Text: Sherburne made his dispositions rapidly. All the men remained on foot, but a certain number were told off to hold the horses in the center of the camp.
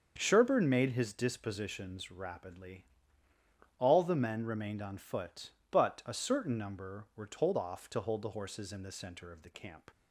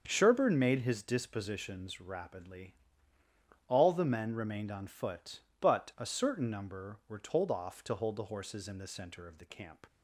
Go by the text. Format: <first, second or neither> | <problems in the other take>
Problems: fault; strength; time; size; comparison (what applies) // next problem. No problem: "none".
neither | starts louder than the rest; the same in both